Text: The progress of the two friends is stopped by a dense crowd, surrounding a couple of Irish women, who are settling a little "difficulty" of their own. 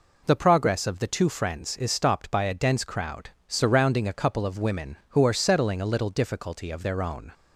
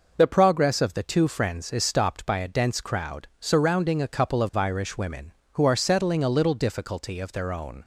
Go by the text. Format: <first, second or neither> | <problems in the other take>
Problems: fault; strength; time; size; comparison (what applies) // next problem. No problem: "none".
second | skips "Irish"; at 4.5 s